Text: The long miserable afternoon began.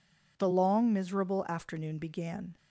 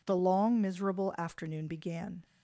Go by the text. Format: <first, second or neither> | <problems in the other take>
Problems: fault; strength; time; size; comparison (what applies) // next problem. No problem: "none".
neither | none